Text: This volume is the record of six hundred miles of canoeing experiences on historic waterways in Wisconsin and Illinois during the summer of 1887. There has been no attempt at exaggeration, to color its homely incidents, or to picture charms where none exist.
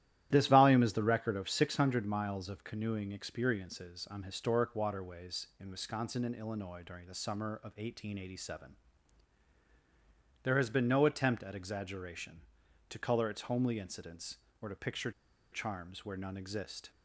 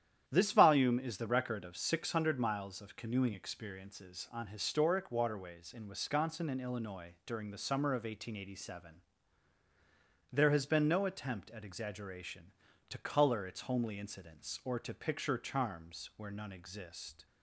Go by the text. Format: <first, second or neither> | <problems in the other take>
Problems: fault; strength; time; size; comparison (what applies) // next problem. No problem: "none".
second | starts louder than the rest; strong; until 1.3 s; 13 dB; strong in the second // pauses between "picture" and "charms"; at 15.1 s; 0.40 s long